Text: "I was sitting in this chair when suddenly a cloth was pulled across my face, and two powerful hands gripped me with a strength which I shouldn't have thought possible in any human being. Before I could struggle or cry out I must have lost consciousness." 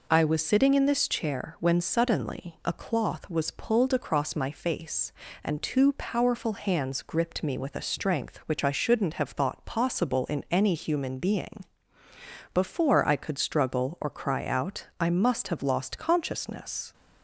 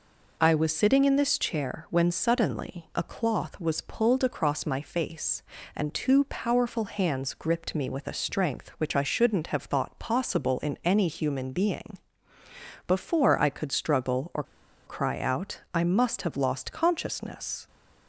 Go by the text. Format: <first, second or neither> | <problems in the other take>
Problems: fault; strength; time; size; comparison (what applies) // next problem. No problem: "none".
first | pauses between "or" and "cry"; at 14.4 s; 0.43 s long